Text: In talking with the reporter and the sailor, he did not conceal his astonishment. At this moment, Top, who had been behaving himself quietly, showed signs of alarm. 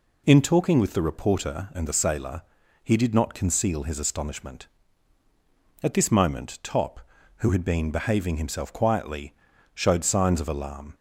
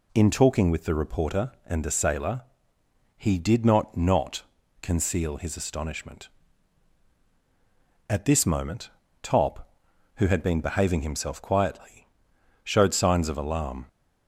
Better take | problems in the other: first | says "not" twice; at 3.9 s

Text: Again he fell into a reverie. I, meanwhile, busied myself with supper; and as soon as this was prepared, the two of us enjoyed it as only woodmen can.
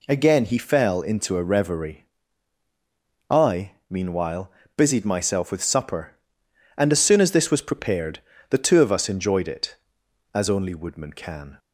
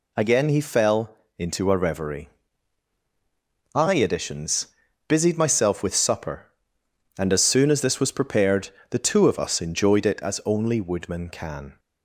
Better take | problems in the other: first | pauses between "fell" and "into"; slight; at 1.1 s; 0.24 s long // says "editions" for "meanwhile"; at 3.9 s

